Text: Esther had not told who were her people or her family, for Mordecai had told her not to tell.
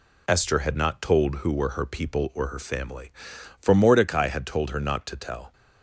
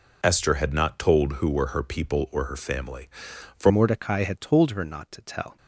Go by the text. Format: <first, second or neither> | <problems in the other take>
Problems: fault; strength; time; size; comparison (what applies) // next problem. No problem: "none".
first | changes voice at "Mordecai"; from 3.6 s on; 1.9 s long